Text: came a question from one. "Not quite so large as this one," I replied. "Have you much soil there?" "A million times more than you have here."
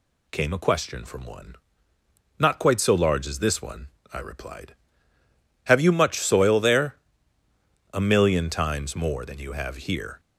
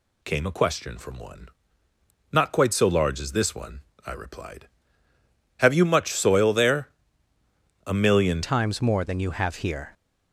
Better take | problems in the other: first | changes voice at "times"; from 8.4 s on; 1.5 s long

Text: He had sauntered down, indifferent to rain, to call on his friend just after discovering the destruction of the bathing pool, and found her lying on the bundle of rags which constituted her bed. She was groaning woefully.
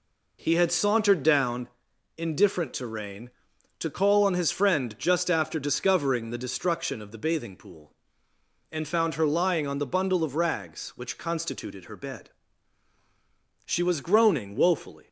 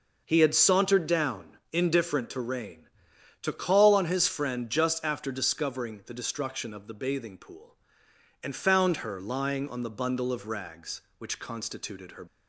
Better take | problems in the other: first | stops before "bed She was groaning woefully"; at 12.2 s

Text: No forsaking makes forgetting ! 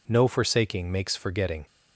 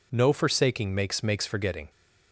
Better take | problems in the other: first | says "makes" twice; at 1.2 s

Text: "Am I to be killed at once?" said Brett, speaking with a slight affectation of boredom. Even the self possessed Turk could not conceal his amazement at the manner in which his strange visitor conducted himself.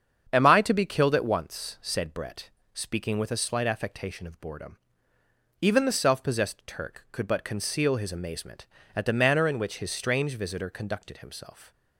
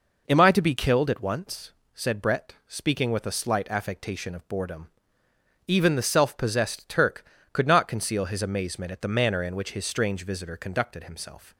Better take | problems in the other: second | starts louder than the rest; strong; until 1.3 s; 7.5 dB // says "but" for "not"; at 7.2 s

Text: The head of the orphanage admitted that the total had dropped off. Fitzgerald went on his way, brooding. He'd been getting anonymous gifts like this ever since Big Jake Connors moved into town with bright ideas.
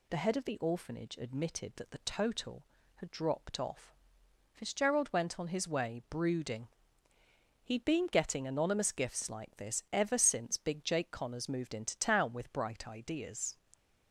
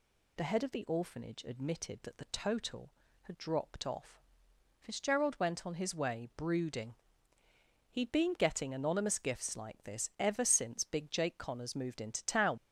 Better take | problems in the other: first | stops before "with bright ideas"; at 12.5 s

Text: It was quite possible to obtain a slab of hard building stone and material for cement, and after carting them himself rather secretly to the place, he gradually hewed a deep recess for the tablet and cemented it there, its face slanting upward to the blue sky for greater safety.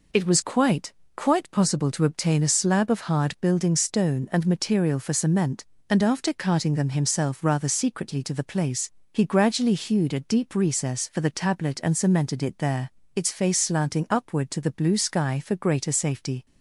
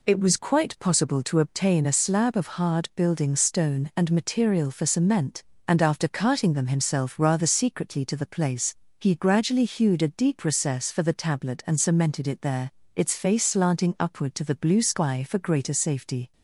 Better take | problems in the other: second | says "quite" twice; at 1.1 s

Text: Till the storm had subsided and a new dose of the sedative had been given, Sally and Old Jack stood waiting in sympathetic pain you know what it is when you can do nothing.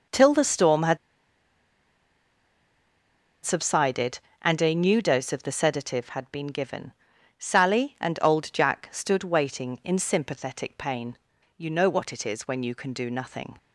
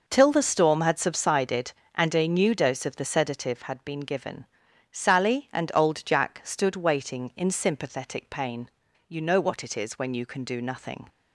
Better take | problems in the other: second | pauses between "had" and "subsided"; strong; at 0.9 s; 2.4 s long // pauses between "pain" and "you"; at 11.1 s; 0.38 s long; also in the second

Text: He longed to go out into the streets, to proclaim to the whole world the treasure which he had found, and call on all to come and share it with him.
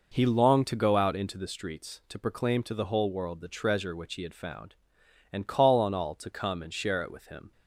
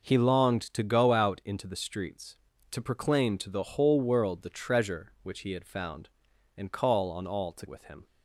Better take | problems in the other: first | starts louder than the rest; until 1.2 s; 6.5 dB // skips "come and share it"; at 7.6 s

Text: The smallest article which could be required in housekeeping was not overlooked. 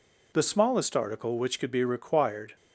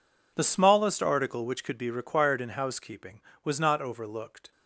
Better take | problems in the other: second | stops before "in housekeeping was not overlooked"; at 2.5 s

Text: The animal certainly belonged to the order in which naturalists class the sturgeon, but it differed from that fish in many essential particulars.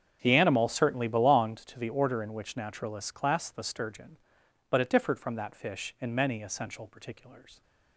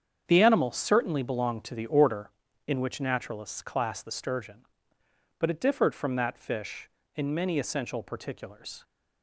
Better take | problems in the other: neither | starts louder than the rest; strong; the same in both

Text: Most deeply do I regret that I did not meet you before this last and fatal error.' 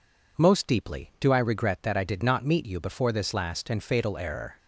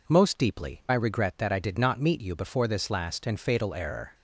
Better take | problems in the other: first | skips "do"; at 0.8 s

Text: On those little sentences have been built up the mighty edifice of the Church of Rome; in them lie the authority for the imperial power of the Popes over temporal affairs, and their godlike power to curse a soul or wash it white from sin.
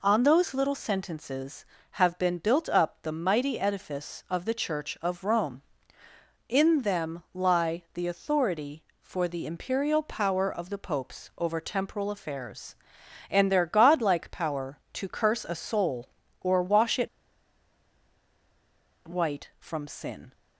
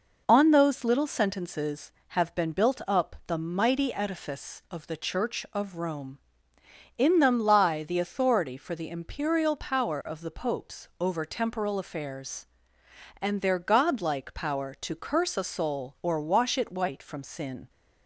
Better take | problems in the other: second | pauses between "it" and "white"; strong; at 17.0 s; 1.9 s long

